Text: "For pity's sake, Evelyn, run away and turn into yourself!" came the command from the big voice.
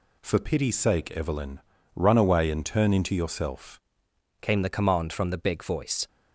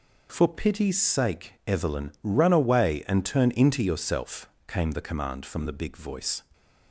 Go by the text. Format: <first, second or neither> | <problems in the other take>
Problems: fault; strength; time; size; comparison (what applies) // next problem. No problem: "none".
second | changes voice at "came"; from 4.4 s on; 1.6 s long